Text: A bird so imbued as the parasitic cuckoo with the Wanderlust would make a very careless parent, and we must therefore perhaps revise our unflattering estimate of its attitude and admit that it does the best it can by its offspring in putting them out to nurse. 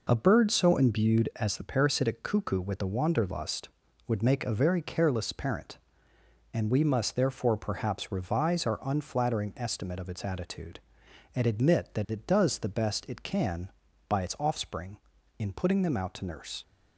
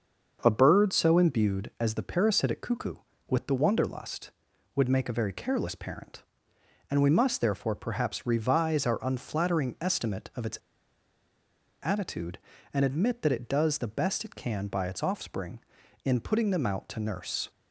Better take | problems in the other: first | starts louder than the rest; until 1.4 s; 6.5 dB // pauses between "its" and "attitude"; strong; at 10.5 s; 1.2 s long

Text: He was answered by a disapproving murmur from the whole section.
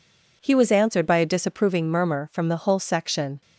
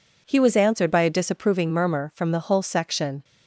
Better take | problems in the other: neither | none

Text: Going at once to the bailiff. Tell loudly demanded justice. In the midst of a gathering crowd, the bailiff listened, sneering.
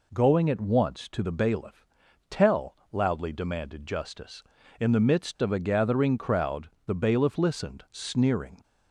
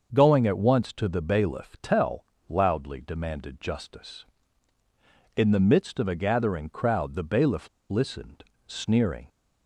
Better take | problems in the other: first | starts louder than the rest; until 1.1 s; 6.5 dB // pauses between "Tell" and "loudly"; slight; at 2.2 s; 0.24 s long; slight in the first // pauses between "bailiff" and "listened"; slight; at 7.6 s; 0.21 s long

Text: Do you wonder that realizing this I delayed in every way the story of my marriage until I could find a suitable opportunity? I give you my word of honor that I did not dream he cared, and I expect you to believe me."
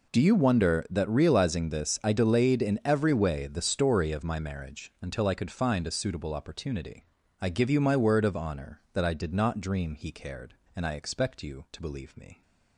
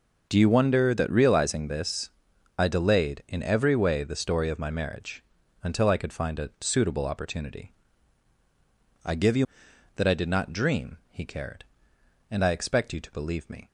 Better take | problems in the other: first | pauses between "this" and "I"; noticeable; at 2.1 s; 0.48 s long // pauses between "marriage" and "until"; at 5.2 s; 0.40 s long // skips "my word of honor"; at 9.7 s

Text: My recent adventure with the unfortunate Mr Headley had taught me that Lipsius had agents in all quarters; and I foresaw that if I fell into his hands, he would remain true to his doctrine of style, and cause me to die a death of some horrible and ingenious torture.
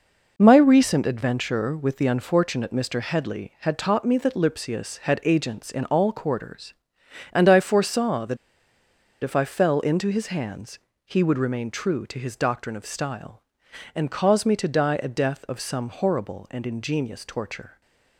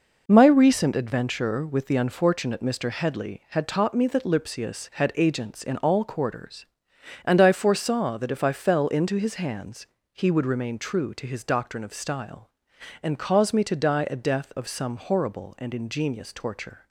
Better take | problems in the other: second | pauses between "that" and "if"; noticeable; at 8.3 s; 0.87 s long

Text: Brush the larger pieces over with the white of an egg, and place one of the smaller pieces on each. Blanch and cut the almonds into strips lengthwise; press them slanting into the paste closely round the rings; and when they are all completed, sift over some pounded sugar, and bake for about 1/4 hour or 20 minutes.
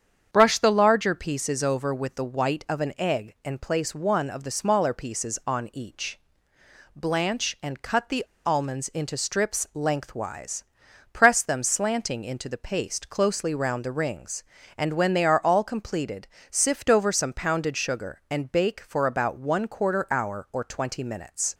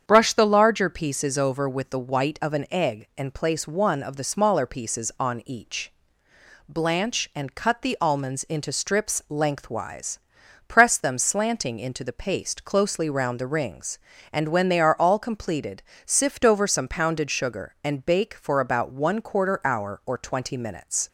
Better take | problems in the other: second | starts louder than the rest; strong; until 1.3 s; 8 dB; strong in the second // pauses between "the" and "almonds"; slight; at 8.2 s; 0.20 s long

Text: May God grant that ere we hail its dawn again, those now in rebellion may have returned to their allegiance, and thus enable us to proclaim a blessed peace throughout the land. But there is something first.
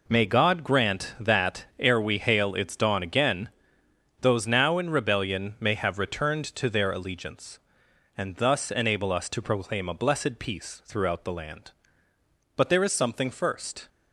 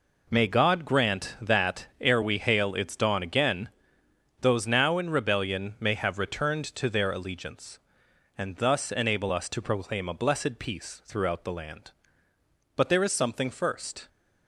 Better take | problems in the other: neither | pauses between "that" and "ere"; slight; the same in both

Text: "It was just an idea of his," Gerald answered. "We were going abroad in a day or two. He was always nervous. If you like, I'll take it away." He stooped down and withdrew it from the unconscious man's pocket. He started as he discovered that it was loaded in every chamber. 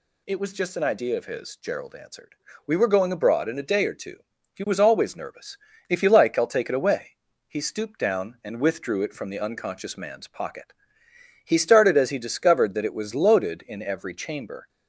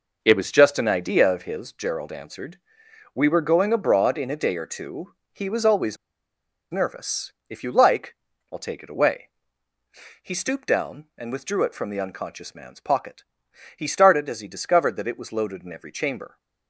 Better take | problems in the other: first | pauses between "always" and "nervous"; noticeable; at 5.9 s; 0.74 s long

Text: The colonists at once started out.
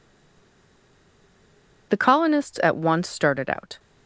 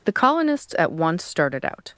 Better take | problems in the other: second | stays silent before the first word; noticeable; until 1.8 s; 1.8 s long

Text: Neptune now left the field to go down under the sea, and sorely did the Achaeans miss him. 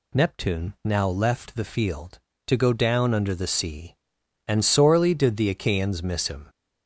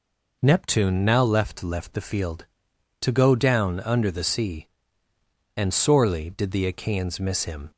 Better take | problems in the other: first | says "left" twice; at 1.6 s

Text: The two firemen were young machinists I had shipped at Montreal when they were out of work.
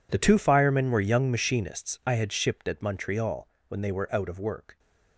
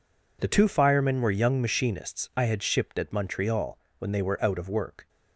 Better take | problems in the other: second | gets quieter; strong; throughout; 18 dB // pauses between "Montreal" and "when"; slight; at 3.4 s; 0.20 s long; slight in the second

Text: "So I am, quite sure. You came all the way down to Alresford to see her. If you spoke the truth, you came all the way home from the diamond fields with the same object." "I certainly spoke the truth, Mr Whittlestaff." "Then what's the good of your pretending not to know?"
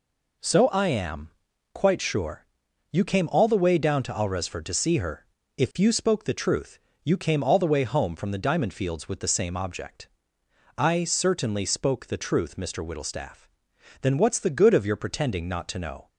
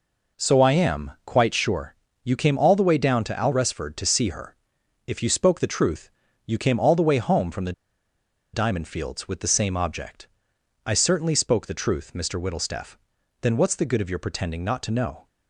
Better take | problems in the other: first | pauses between "the" and "diamond"; noticeable; at 7.7 s; 0.81 s long

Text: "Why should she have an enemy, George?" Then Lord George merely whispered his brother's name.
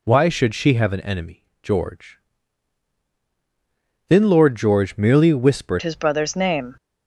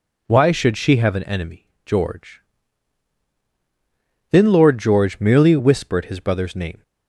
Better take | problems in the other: second | changes voice at "his"; from 5.8 s on; 0.9 s long

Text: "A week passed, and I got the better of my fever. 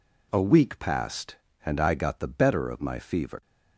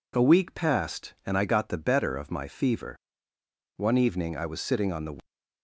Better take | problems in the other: first | goes on to say "One evening I was sitting on the"; from 3.7 s on; 1.4 s long

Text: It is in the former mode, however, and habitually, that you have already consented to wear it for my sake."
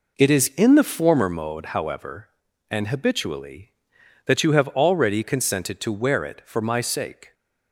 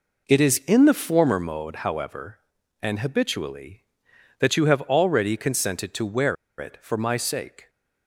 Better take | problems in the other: first | pauses between "wear" and "it"; slight; at 6.3 s; 0.23 s long

